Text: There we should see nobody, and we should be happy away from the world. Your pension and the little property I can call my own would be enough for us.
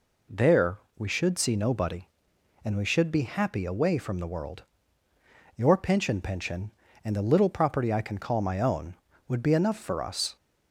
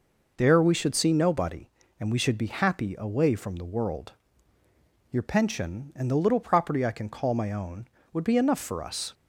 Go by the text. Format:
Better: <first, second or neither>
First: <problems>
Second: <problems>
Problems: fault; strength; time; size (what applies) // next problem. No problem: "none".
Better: second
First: pauses between "There" and "we"; slight; at 0.7 s; 0.20 s long // says "pension" twice; at 6.2 s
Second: none